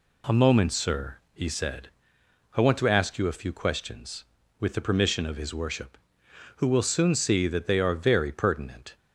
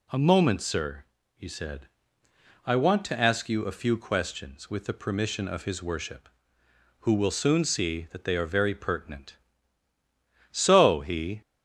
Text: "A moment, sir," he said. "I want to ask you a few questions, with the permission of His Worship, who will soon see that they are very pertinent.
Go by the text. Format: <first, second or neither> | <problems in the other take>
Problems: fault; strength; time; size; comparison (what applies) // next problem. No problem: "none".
first | goes on to say "So he"; noticeable; from 10.5 s on; 0.90 s long